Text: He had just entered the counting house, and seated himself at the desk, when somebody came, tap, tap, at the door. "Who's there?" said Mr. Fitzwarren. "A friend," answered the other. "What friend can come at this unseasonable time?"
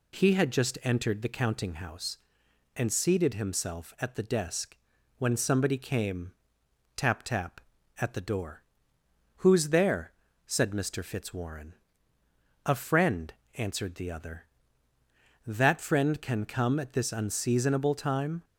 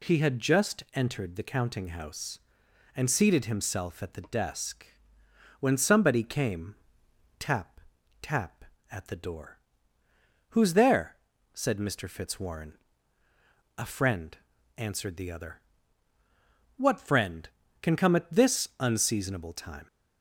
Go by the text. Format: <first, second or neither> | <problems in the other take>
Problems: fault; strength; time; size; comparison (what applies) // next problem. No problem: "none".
second | says "That" for "What"; at 15.4 s